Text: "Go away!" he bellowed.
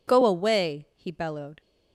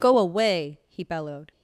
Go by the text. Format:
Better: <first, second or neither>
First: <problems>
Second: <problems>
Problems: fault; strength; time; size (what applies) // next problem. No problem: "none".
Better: neither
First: none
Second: none